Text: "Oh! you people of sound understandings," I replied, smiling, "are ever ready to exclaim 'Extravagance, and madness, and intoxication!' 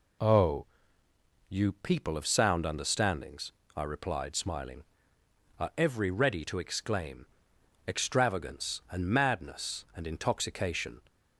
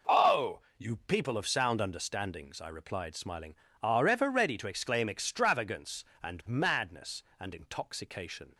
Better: second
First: says "every" for "ever"; at 5.7 s // pauses between "exclaim" and "Extravagance"; noticeable; at 7.2 s; 0.62 s long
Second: none

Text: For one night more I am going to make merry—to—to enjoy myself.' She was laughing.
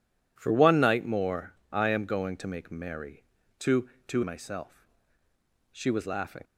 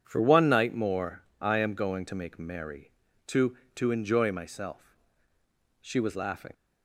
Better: second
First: pauses between "more" and "I"; slight; at 1.5 s; 0.20 s long // skips "enjoy"; at 4.2 s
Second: pauses between "more" and "I"; slight; at 1.2 s; 0.20 s long

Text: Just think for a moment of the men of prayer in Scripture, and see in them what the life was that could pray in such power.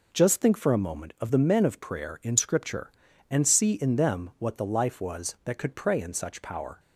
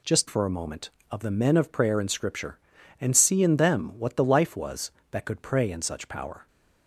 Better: first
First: none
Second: skips "think"; at 0.2 s

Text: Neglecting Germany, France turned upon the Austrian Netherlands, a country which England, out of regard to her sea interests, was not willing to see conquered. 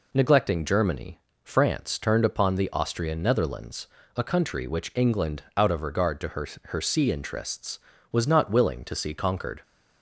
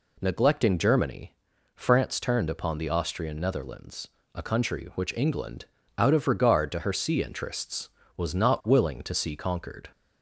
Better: second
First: says "her" twice; at 6.6 s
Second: none

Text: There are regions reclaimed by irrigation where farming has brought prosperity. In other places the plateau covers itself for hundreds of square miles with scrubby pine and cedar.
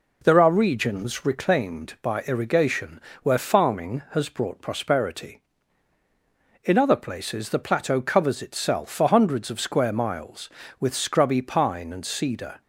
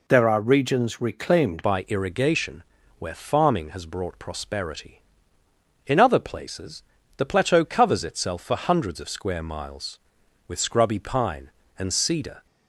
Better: first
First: pauses between "irrigation" and "where"; slight; at 3.0 s; 0.24 s long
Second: changes voice at "by"; from 1.6 s on; 10.8 s long // pauses between "irrigation" and "where"; slight; at 2.6 s; 0.36 s long // pauses between "places" and "the"; slight; at 6.8 s; 0.36 s long

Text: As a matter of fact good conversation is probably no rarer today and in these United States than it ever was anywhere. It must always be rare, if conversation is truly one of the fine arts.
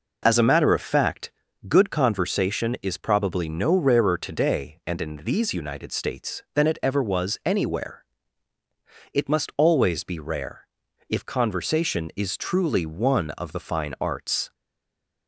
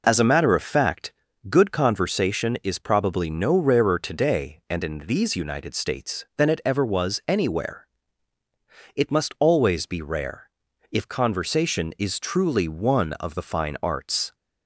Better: second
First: pauses between "fact" and "good"; slight; at 1.3 s; 0.36 s long // stays silent after the last word; slight; from 14.5 s on; 0.7 s long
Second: pauses between "fact" and "good"; slight; at 1.1 s; 0.36 s long

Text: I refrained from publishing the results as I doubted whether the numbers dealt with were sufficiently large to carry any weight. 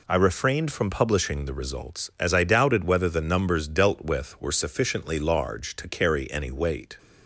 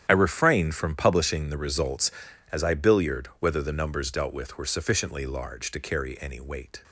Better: first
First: none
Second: starts louder than the rest; strong; until 1.1 s; 10 dB // says "billiard" for "doubted"; at 2.7 s

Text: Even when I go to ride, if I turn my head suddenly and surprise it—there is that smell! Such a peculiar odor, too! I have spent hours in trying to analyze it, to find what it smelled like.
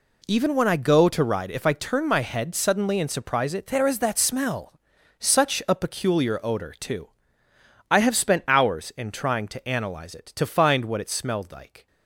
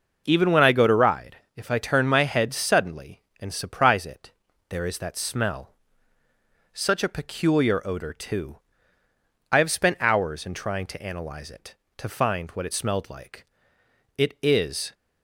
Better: first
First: none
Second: goes on to say "It is"; noticeable; from 14.1 s on; 0.78 s long

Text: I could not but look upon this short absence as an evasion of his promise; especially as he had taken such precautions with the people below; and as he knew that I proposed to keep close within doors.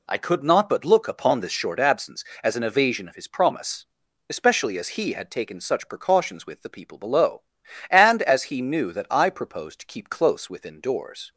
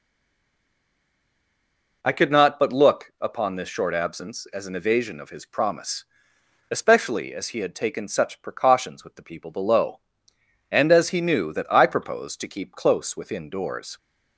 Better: first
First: none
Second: stays silent before the first word; noticeable; until 2.0 s; 2.0 s long

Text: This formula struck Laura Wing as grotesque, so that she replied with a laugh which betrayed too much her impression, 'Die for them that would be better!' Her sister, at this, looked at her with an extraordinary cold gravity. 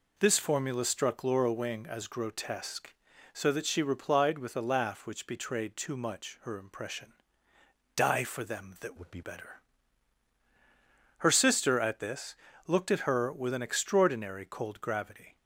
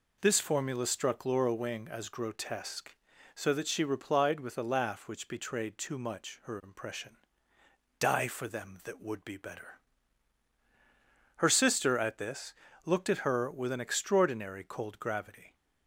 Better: second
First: changes voice from "would" to "be"; from 8.9 to 9.2 s; 0.3 s long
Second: none

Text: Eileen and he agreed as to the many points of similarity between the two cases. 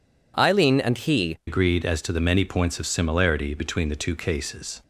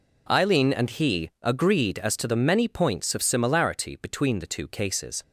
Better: second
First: changes voice at "agreed"; from 1.4 s on; 3.4 s long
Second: none

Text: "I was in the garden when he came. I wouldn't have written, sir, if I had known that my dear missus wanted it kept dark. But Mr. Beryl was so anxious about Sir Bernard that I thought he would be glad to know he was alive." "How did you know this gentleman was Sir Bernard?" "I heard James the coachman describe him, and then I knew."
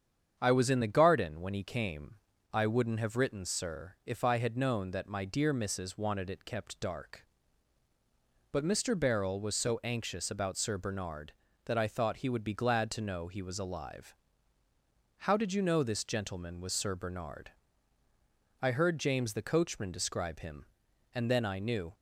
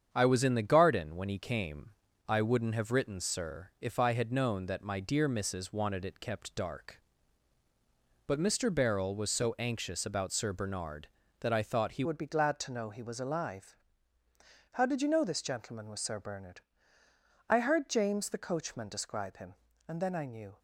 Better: first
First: starts louder than the rest; strong; until 1.4 s; 8 dB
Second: starts louder than the rest; strong; until 1.1 s; 8 dB // changes voice at "would"; from 12.0 s on; 8.5 s long

